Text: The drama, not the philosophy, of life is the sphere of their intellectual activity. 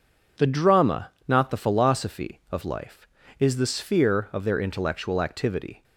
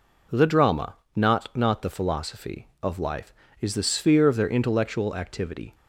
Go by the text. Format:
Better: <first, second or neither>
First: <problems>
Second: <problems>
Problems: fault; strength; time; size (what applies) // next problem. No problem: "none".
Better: first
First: none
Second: says "not" twice; at 1.5 s